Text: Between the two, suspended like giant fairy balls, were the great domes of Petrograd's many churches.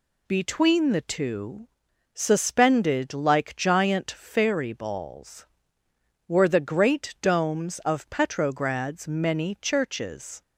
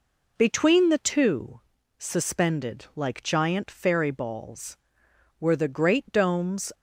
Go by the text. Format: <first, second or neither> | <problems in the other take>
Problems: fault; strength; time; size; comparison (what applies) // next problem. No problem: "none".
first | stops before "of Petrograd's many churches"; at 6.7 s